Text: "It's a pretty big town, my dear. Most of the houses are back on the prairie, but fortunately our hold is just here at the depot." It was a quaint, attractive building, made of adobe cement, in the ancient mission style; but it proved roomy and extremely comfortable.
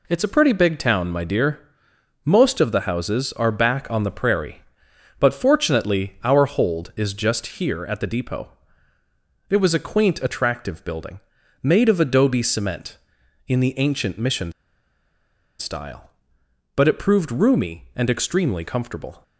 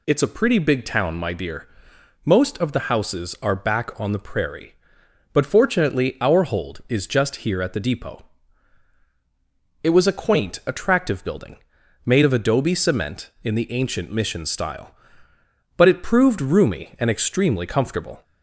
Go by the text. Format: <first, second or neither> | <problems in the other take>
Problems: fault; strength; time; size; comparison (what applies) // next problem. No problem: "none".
second | pauses between "mission" and "style"; at 14.5 s; 1.0 s long